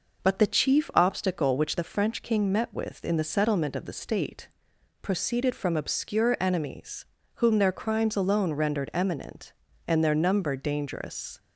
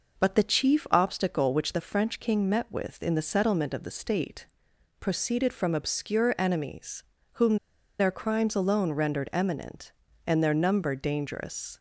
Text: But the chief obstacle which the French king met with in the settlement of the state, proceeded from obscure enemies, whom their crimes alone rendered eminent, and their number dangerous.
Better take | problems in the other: first | pauses between "whom" and "their"; at 7.5 s; 0.42 s long

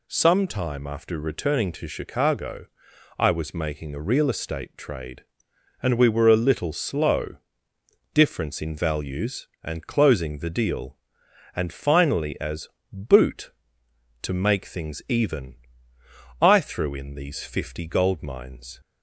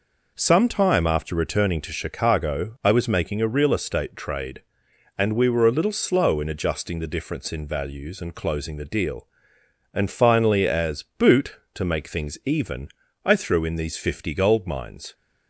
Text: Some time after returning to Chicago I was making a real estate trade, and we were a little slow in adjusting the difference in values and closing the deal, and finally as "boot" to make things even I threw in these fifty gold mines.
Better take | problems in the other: second | pauses between "Chicago" and "I"; noticeable; at 2.6 s; 0.52 s long // skips "in adjusting the"; at 7.7 s // pauses between "as" and "boot"; slight; at 12.6 s; 0.24 s long; slight in the second // pauses between "even" and "I"; noticeable; at 15.5 s; 0.84 s long; slight in the second

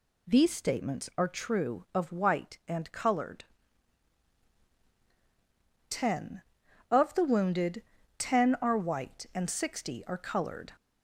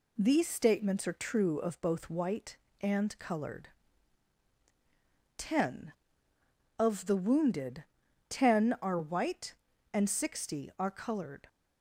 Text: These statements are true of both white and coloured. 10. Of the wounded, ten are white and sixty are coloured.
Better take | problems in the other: second | skips "both"; at 2.1 s

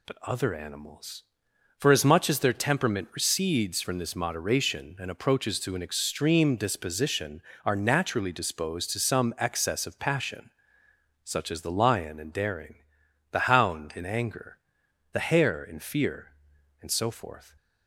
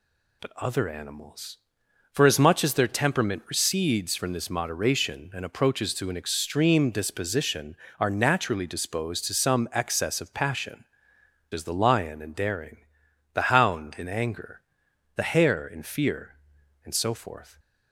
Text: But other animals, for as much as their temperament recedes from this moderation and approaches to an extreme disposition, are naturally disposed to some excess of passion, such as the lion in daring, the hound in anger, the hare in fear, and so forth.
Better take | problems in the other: first | skips "such"; at 11.1 s

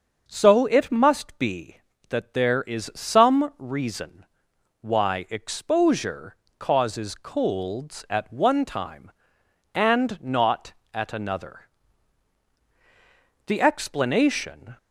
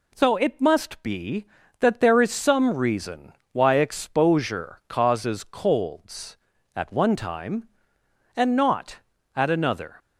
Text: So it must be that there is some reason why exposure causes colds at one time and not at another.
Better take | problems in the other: second | starts louder than the rest; until 1.2 s; 6.5 dB // pauses between "reason" and "why"; noticeable; at 4.2 s; 0.56 s long; slight in the second // pauses between "exposure" and "causes"; slight; at 6.3 s; 0.24 s long // goes on to say "The explanation"; noticeable; from 13.4 s on; 1.3 s long

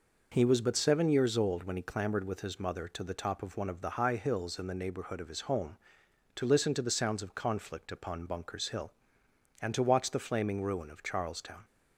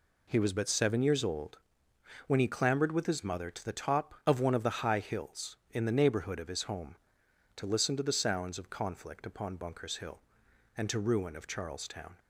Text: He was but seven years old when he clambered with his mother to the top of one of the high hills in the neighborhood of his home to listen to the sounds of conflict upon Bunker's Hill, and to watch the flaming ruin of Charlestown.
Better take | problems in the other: first | pauses between "old" and "when"; noticeable; at 1.5 s; 0.70 s long // skips "watch the flaming"; at 10.9 s

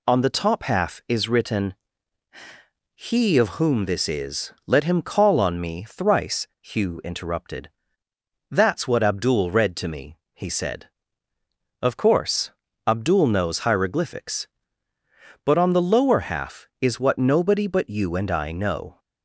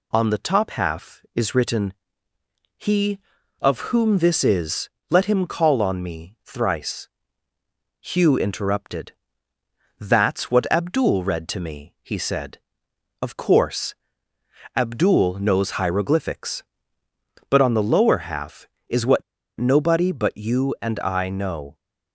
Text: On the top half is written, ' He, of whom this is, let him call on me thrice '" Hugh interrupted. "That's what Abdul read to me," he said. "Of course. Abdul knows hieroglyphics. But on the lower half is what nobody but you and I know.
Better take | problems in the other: first | pauses between "what" and "nobody"; slight; at 19.2 s; 0.34 s long

